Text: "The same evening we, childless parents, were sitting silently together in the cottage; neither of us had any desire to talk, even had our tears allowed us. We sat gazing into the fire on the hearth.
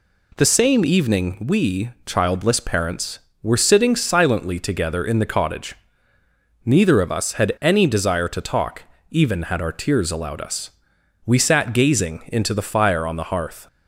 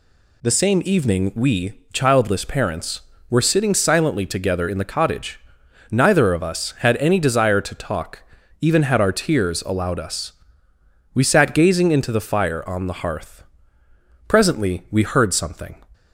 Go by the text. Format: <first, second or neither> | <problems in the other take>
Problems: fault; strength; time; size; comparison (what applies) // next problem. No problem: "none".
first | goes on to say "Presently we heard something"; from 14.2 s on; 1.5 s long